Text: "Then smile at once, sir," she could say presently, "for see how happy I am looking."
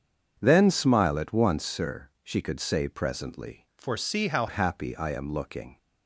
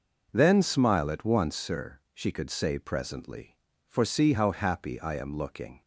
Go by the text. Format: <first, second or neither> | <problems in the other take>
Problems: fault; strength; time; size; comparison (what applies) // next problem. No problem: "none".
second | starts louder than the rest; until 1.3 s; 7 dB // changes voice from "for" to "how"; from 3.7 to 4.4 s; 0.7 s long